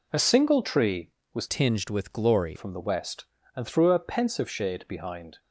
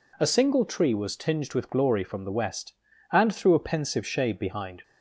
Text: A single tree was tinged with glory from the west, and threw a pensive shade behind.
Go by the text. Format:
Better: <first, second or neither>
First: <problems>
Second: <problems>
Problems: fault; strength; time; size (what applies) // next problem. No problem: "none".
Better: second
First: changes voice from "tinged" to "glory"; from 1.4 to 2.5 s; 1.1 s long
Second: none